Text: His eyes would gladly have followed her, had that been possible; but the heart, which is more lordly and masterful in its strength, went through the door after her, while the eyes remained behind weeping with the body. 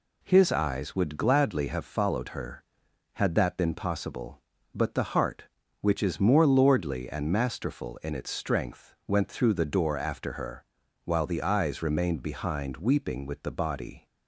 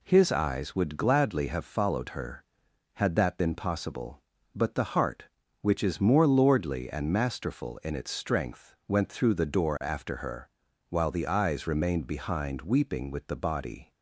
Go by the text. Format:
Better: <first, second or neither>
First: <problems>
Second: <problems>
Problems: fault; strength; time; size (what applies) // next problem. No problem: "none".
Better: neither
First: none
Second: none